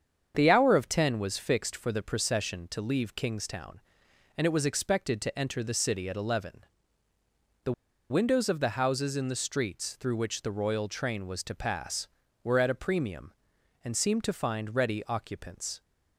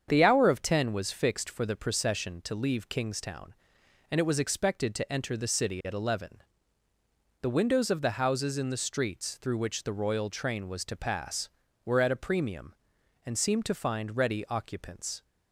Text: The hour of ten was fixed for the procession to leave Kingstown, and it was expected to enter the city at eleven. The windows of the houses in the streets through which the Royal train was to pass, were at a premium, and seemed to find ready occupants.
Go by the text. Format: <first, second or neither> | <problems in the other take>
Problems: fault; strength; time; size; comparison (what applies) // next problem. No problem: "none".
second | starts louder than the rest; strong; until 1.3 s; 7.5 dB; strong in the second // pauses between "The" and "windows"; at 7.7 s; 0.38 s long